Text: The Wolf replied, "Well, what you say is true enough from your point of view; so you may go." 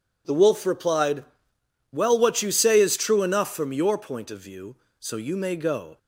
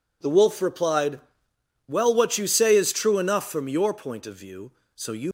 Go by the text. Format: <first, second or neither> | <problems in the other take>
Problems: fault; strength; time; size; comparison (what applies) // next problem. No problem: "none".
first | stops before "may go"; at 5.2 s